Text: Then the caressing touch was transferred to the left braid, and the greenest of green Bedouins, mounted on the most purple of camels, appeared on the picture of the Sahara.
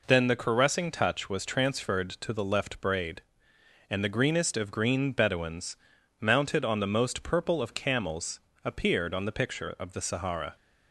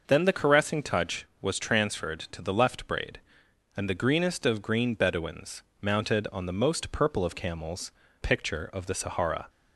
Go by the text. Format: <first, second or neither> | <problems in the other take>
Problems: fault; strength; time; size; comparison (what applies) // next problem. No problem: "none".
first | skips "appeared on the"; at 8.0 s